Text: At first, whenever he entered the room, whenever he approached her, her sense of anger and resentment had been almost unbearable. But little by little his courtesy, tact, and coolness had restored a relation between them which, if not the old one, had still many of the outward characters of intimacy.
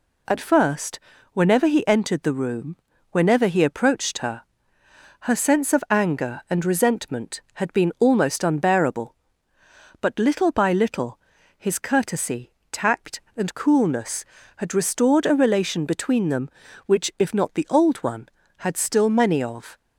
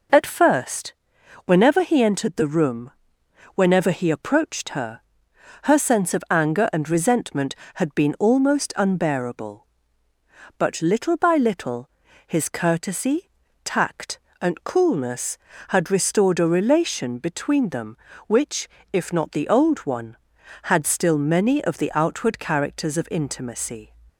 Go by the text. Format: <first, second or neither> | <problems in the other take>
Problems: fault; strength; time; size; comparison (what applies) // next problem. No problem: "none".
second | pauses between "little" and "his"; at 11.1 s; 0.38 s long; also in the second // stops before "the outward characters of intimacy"; at 19.7 s